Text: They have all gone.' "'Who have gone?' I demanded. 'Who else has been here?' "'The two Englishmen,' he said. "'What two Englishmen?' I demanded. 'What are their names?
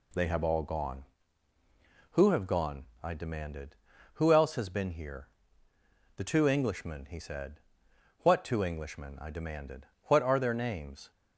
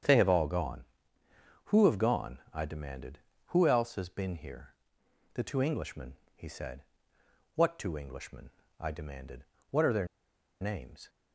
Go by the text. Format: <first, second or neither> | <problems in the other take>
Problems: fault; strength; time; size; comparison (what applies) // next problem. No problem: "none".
first | starts louder than the rest; strong; until 1.8 s; 8 dB // pauses between "their" and "names"; noticeable; at 10.0 s; 0.54 s long